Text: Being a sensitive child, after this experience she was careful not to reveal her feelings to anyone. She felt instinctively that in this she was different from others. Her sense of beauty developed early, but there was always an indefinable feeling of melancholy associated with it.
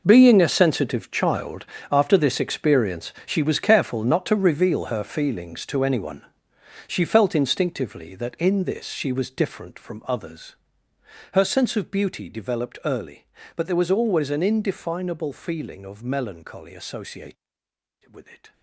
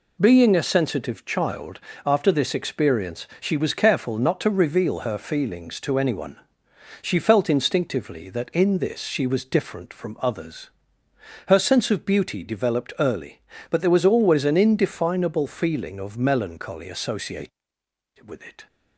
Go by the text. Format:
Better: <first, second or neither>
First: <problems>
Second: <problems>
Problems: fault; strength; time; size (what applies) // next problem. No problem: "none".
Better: second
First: gets quieter; strong; throughout; 13.5 dB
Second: none